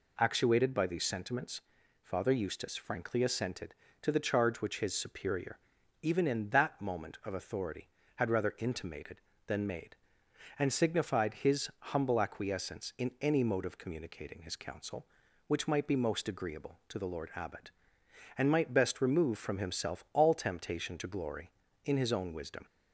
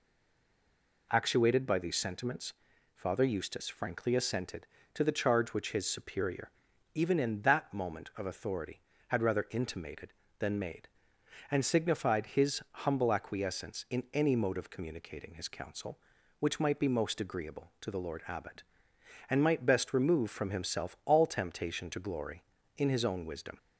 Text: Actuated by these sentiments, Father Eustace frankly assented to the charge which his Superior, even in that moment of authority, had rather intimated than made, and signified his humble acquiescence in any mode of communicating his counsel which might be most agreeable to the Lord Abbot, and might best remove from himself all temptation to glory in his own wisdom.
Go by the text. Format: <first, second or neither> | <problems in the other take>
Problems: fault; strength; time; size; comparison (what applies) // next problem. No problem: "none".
first | stays silent before the first word; until 1.1 s; 1.1 s long